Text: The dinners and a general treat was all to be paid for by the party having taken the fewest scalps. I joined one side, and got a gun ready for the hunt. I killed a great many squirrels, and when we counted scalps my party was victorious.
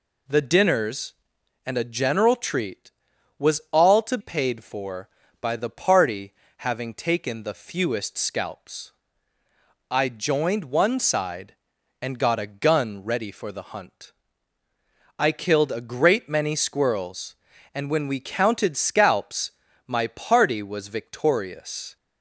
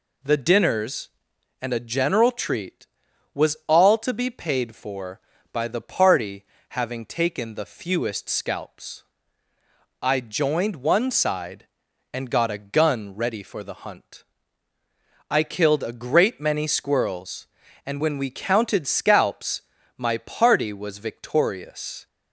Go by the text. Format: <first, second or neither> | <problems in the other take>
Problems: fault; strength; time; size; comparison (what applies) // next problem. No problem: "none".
second | skips "be"; at 4.1 s // pauses between "party" and "having"; slight; at 6.3 s; 0.26 s long; slight in the second // pauses between "scalps" and "my"; slight; at 19.4 s; 0.36 s long; slight in the second